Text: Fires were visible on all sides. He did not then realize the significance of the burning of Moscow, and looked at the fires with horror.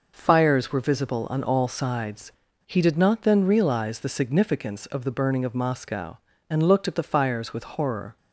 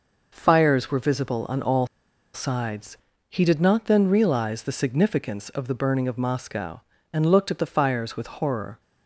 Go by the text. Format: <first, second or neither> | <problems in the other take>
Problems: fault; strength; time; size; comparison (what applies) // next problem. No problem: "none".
first | pauses between "all" and "sides"; noticeable; at 1.8 s; 0.46 s long